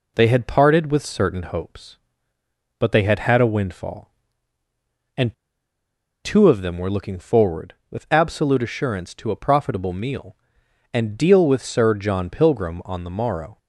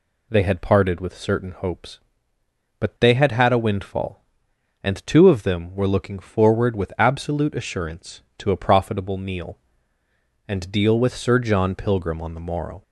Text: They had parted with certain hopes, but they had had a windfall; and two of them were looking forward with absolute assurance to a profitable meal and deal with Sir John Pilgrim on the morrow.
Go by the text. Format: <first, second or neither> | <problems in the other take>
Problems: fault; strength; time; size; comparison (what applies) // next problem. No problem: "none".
second | pauses between "and" and "two"; noticeable; at 5.3 s; 0.89 s long